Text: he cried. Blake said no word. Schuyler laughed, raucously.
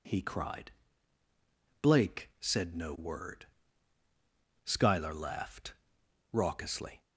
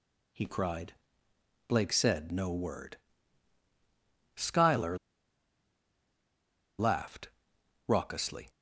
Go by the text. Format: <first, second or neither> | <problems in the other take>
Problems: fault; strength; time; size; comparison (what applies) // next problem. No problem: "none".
first | pauses between "Schuyler" and "laughed"; strong; at 4.9 s; 1.8 s long